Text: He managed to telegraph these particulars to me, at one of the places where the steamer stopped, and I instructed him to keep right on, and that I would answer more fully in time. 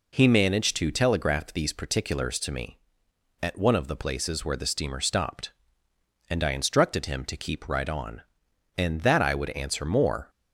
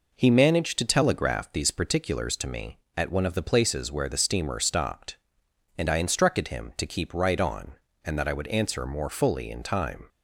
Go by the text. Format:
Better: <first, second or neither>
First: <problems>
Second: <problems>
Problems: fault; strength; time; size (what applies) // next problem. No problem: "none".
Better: second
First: stops before "fully in time"; at 10.2 s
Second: none